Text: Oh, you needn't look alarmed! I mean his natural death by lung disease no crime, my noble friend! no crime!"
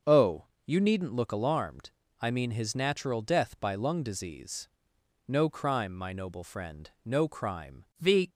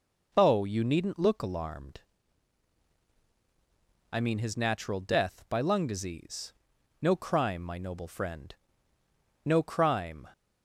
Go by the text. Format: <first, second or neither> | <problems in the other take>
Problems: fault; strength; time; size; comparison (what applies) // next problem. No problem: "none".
second | starts louder than the rest; until 1.2 s; 6 dB // pauses between "disease" and "no"; noticeable; at 4.6 s; 0.58 s long; noticeable in the second // goes on to say "The"; slight; from 8.0 s on; 0.28 s long